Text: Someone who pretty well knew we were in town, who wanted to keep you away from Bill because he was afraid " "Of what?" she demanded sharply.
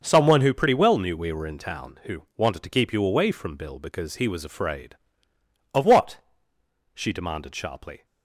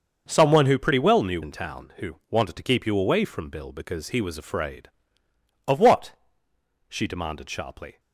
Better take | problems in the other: first | starts louder than the rest; until 1.2 s; 6.5 dB; also in the first // skips "we were"; at 1.4 s

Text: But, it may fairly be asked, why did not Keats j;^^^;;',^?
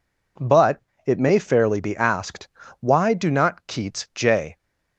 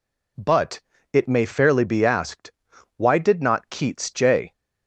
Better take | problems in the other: second | says "do" for "did"; at 3.1 s

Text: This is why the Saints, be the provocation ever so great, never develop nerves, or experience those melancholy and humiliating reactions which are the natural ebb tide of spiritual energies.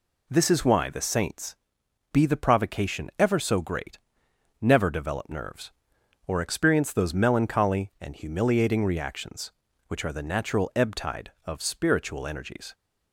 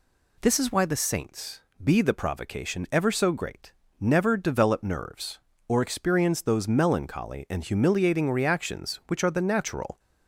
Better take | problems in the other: first | stops before "ebb tide of spiritual energies"; at 9.9 s

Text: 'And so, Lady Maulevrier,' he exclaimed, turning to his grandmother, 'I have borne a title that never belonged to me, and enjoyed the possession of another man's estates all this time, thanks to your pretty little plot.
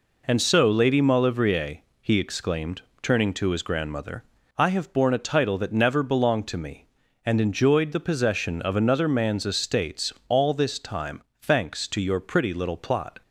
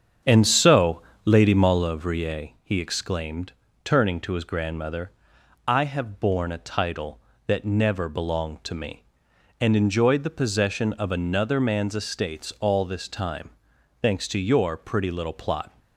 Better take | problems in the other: first | starts louder than the rest; strong; until 1.9 s; 7.5 dB

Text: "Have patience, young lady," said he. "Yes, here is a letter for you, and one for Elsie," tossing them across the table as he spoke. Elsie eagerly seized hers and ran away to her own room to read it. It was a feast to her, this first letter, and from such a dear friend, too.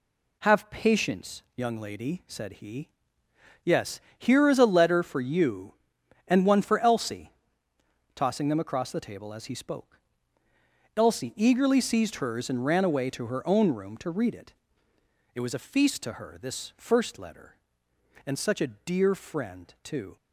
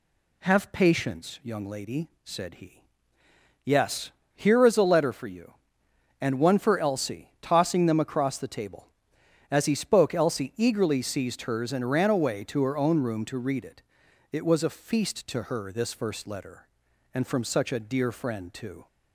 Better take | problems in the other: second | skips "from"; at 18.3 s

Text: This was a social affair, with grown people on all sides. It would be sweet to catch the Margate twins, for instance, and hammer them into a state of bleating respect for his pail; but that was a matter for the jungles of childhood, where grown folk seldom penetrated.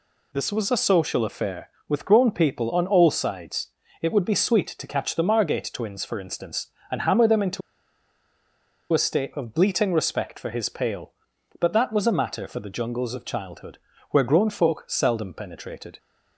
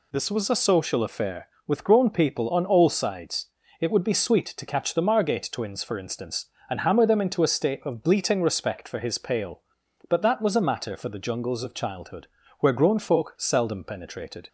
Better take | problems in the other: second | pauses between "into" and "a"; strong; at 7.6 s; 1.3 s long

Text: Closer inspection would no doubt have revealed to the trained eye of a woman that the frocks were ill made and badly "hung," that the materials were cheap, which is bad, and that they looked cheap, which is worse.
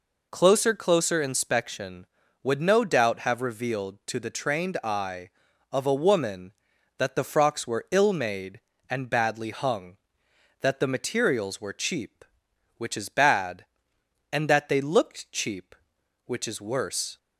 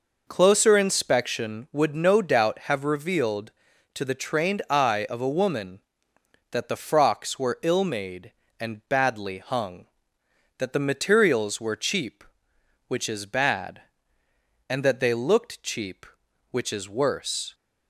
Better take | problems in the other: second | says "Closer" twice; at 0.7 s

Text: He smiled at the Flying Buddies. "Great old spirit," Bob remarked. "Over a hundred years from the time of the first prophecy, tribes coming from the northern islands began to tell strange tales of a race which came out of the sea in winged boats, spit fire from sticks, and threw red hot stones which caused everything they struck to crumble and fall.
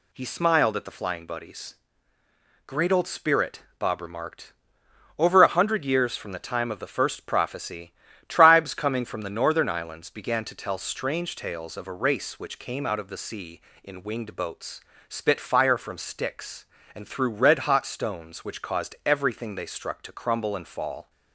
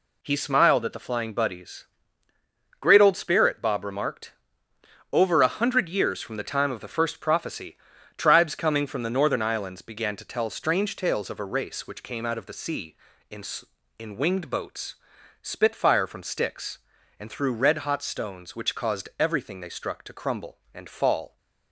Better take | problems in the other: first | says "in" twice; at 13.9 s

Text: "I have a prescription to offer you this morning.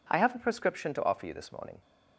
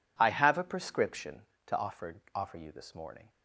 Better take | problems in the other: first | says "offer" twice; at 2.3 s

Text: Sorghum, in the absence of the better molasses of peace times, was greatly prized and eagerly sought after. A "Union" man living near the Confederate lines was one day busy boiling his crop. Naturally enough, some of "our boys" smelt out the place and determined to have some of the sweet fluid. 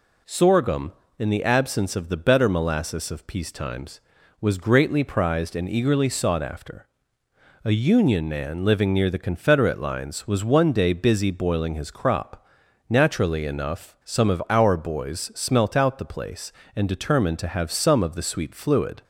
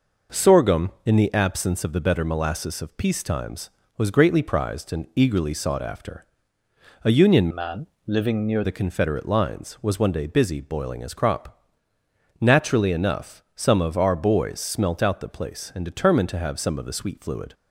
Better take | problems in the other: first | changes voice from "man" to "near"; from 7.5 to 8.6 s; 1.1 s long // pauses between "man" and "living"; slight; at 7.8 s; 0.20 s long

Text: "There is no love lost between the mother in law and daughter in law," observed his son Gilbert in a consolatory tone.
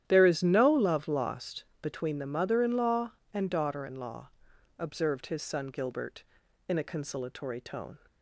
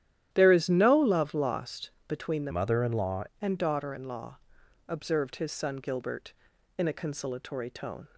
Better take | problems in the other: first | starts louder than the rest; strong; until 1.3 s; 11.5 dB; strong in the first // pauses between "lost" and "between"; slight; at 1.9 s; 0.16 s long; slight in the first // changes voice from "mother" to "law"; from 2.5 to 3.2 s; 0.7 s long

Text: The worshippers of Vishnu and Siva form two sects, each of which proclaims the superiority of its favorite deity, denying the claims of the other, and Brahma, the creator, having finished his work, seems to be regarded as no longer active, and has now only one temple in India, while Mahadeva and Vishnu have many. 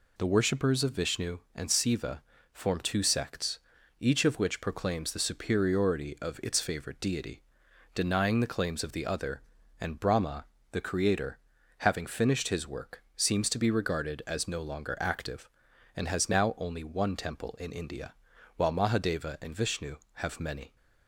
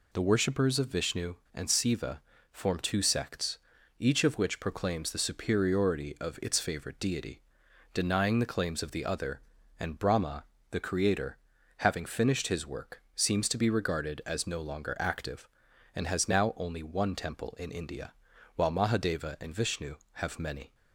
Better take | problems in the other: neither | pauses between "Siva" and "form"; slight; the same in both

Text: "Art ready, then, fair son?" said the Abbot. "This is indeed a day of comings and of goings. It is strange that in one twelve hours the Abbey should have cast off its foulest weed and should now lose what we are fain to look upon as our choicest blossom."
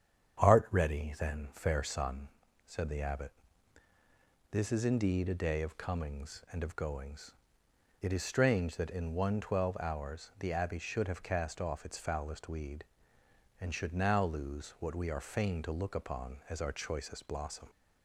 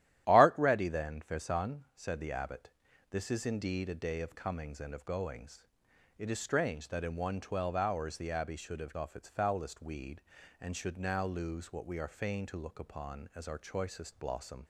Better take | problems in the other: first | starts louder than the rest; strong; until 1.2 s; 12.5 dB; strong in the first // skips "cast"; at 8.9 s

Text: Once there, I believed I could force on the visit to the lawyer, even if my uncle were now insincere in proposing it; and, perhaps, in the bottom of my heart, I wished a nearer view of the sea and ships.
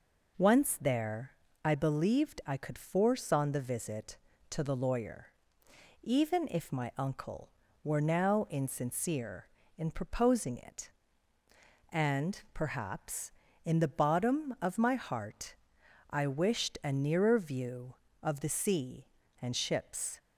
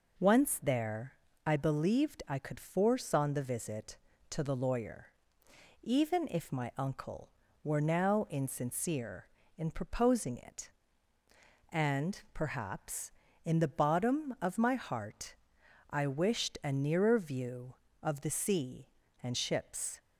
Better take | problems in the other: neither | none

